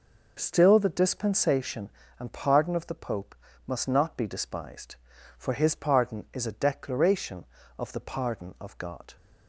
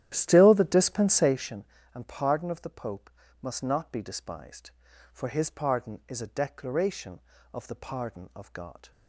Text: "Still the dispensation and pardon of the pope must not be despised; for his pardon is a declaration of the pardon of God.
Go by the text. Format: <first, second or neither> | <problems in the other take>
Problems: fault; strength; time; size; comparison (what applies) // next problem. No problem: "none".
first | starts louder than the rest; strong; until 1.6 s; 12 dB // pauses between "pope" and "must"; slight; at 3.0 s; 0.32 s long; slight in the first